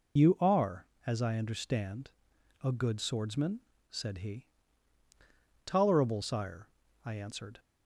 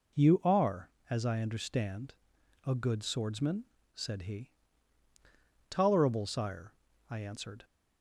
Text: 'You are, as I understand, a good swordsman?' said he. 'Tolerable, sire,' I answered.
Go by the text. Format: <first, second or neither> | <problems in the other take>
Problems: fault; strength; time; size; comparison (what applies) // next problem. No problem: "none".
second | loses the start of "You"; at 0.1 s; 40 ms